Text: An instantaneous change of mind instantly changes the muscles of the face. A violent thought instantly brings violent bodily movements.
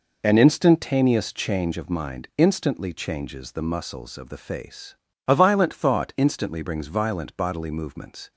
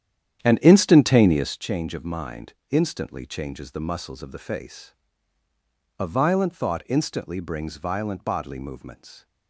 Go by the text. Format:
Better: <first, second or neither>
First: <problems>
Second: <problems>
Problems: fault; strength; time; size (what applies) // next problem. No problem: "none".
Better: first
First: none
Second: starts louder than the rest; strong; until 1.7 s; 10 dB // pauses between "mind" and "instantly"; slight; at 2.5 s; 0.16 s long